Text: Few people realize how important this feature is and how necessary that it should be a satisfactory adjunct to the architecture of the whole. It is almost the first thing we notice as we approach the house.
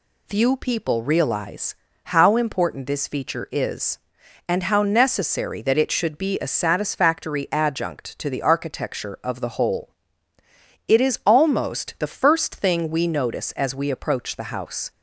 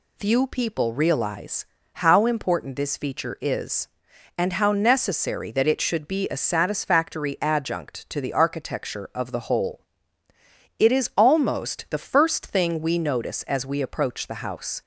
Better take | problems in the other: neither | pauses between "realize" and "how"; slight; the same in both

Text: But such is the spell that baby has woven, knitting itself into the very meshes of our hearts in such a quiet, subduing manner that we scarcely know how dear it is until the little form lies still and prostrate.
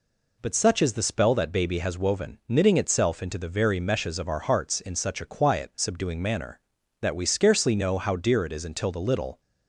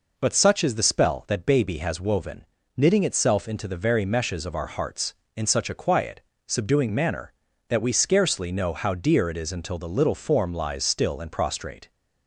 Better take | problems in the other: second | stops before "form lies still and prostrate"; at 9.3 s

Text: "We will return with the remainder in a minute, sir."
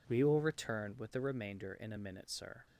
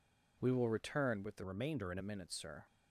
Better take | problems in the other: first | changes voice from "remainder" to "in"; from 1.4 to 1.9 s; 0.5 s long

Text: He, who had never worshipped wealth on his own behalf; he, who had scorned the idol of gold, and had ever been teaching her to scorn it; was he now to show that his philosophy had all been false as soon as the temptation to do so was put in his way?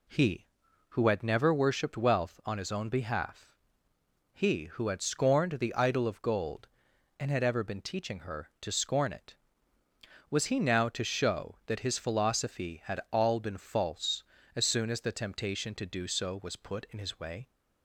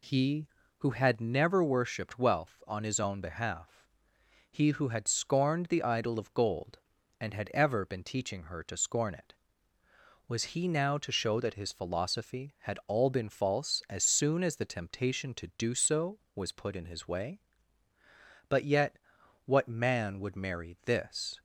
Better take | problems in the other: first | goes on to say "But yet what man would marry this"; strong; from 18.4 s on; 2.9 s long

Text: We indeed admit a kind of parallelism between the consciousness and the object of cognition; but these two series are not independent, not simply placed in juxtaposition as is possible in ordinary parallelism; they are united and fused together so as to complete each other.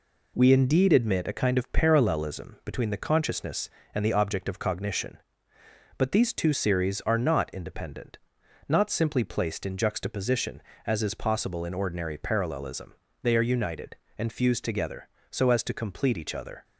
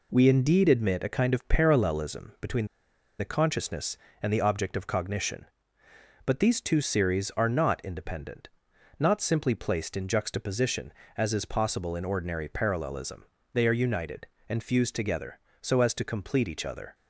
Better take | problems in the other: first | pauses between "between" and "the"; noticeable; at 2.6 s; 0.52 s long

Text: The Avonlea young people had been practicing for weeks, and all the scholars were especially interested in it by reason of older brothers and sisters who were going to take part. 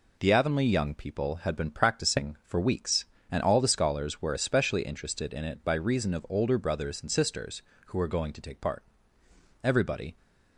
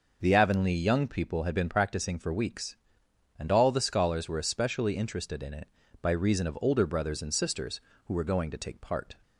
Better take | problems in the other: second | goes on to say "Everybody"; from 9.6 s on; 0.54 s long

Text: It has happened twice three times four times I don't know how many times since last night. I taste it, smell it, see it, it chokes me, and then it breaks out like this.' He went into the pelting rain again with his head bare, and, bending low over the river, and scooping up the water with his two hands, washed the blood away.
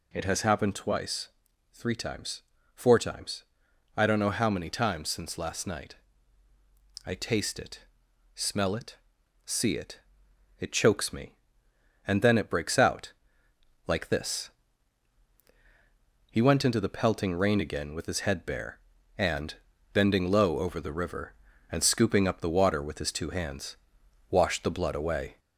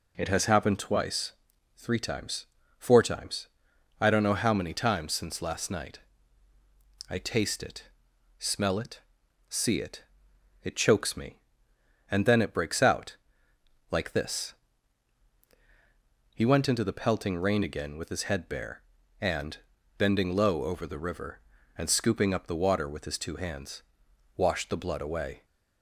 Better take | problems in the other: second | gets louder; slight; throughout; 2 dB // pauses between "twice" and "three"; at 1.2 s; 0.44 s long; also in the second // pauses between "times" and "four"; slight; at 2.4 s; 0.32 s long; slight in the second // pauses between "times" and "I"; noticeable; at 3.4 s; 0.52 s long; noticeable in the second // pauses between "out" and "like"; noticeable; at 13.1 s; 0.74 s long; noticeable in the second

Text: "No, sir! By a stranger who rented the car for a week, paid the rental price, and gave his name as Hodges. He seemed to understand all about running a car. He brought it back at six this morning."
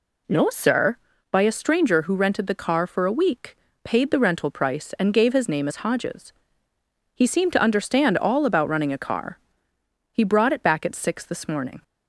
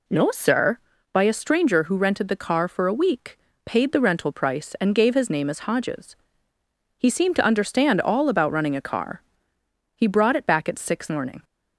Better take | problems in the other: first | skips "this"; at 11.0 s

